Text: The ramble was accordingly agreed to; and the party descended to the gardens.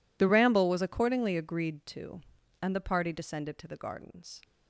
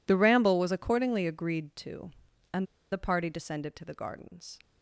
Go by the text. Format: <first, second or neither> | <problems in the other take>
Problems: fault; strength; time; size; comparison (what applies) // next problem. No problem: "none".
first | pauses between "and" and "the"; slight; at 2.6 s; 0.27 s long